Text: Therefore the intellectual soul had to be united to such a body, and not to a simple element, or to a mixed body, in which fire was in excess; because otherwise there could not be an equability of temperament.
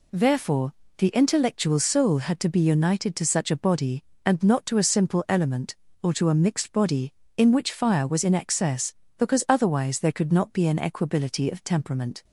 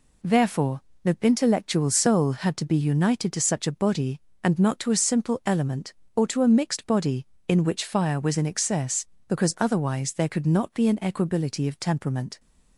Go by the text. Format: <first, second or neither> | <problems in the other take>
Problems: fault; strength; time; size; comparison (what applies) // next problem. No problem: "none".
neither | pauses between "Therefore" and "the"; slight; the same in both